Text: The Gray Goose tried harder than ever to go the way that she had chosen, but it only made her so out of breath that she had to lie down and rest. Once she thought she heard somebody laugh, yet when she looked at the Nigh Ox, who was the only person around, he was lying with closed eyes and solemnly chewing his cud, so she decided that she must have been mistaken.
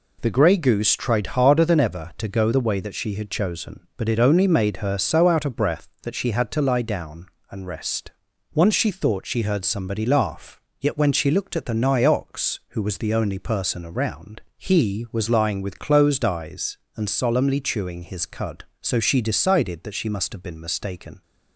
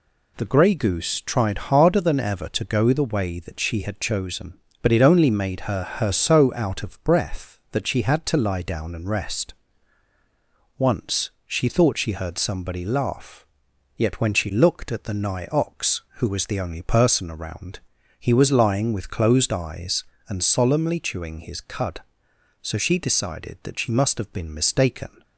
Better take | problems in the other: first | says "her" twice; at 5.8 s // pauses between "Once" and "she"; slight; at 11.2 s; 0.16 s long

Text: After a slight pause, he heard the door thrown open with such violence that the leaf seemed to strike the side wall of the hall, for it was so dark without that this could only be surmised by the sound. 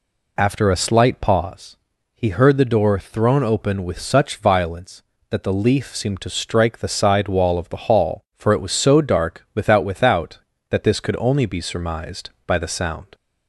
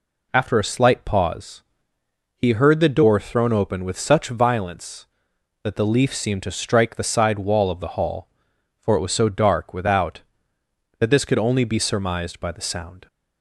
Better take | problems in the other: second | says "without" twice; at 9.8 s

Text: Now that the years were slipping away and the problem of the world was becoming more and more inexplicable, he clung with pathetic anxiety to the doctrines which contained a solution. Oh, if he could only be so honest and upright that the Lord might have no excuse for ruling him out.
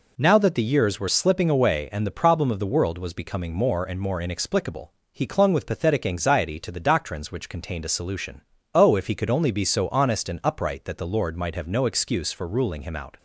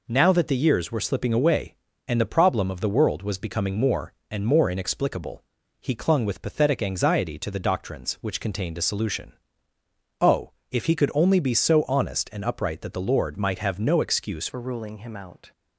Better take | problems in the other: first | changes voice at "for"; from 14.4 s on; 1.1 s long

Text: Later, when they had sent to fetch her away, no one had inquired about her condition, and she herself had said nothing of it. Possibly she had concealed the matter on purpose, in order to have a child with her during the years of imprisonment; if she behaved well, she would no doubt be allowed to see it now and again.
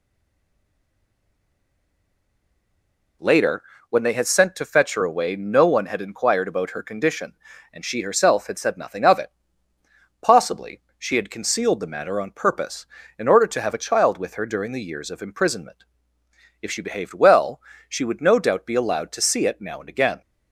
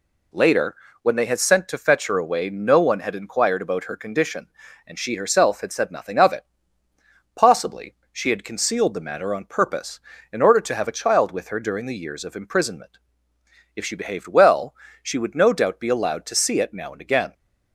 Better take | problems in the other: second | stays silent before the first word; strong; until 3.1 s; 3.1 s long // pauses between "Possibly" and "she"; slight; at 10.8 s; 0.16 s long; slight in the second

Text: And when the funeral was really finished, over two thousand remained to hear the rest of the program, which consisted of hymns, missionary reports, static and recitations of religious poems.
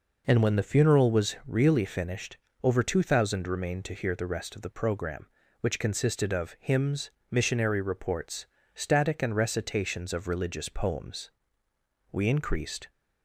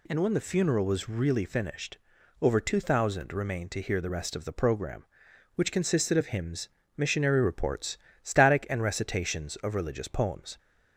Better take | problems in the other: second | goes on to say "We increased"; noticeable; from 12.1 s on; 0.78 s long

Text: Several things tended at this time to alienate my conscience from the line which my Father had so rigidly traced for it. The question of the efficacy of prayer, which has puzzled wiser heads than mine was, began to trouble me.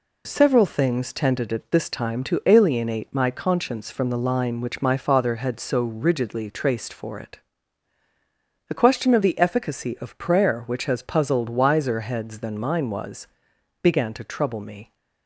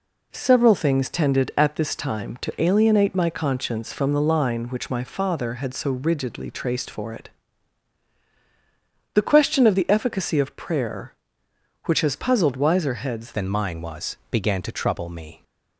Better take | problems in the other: first | changes voice at "than"; from 13.3 s on; 2.1 s long

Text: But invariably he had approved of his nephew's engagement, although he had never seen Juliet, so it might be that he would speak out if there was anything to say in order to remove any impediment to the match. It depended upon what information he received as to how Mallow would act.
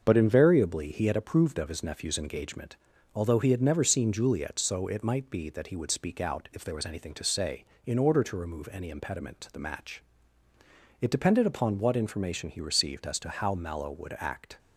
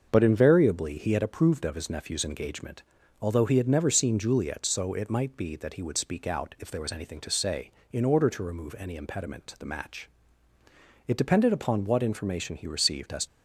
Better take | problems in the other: first | starts louder than the rest; until 1.1 s; 6.5 dB; also in the first // stops before "to how Mallow would act"; at 13.2 s

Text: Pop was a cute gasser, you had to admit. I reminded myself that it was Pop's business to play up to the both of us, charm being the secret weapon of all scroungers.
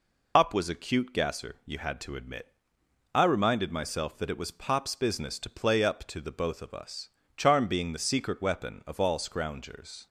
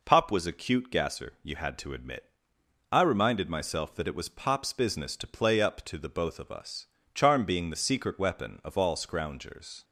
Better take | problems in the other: second | loses the start of "Pop"; at 0.3 s; 90 ms

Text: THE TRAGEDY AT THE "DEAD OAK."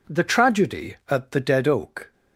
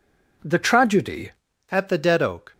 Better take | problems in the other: first | changes voice at "AT"; from 1.7 s on; 0.8 s long

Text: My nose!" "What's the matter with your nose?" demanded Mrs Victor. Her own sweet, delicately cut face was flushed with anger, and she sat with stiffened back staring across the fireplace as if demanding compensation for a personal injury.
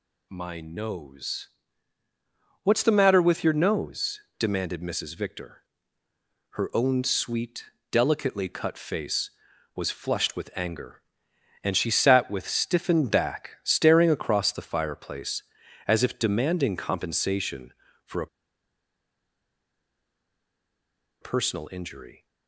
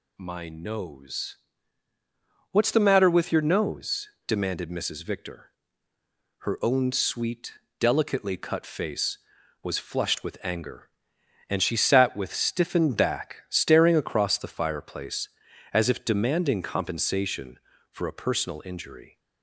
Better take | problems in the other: second | pauses between "a" and "personal"; strong; at 18.2 s; 2.9 s long

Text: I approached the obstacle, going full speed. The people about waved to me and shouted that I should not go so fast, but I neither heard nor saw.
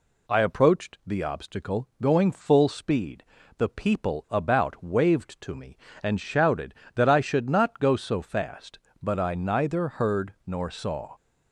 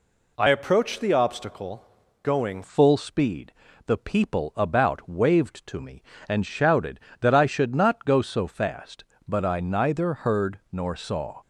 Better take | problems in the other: first | changes voice from "approached" to "going"; from 0.4 to 2.6 s; 2.2 s long

